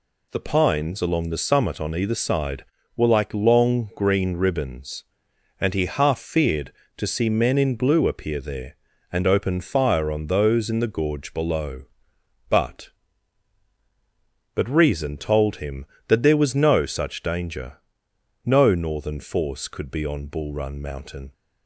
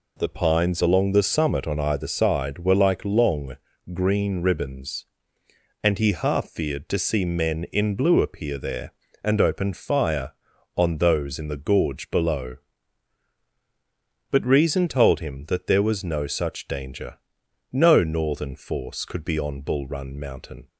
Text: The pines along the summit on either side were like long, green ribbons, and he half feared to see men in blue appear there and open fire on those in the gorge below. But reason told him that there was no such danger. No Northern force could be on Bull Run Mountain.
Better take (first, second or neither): second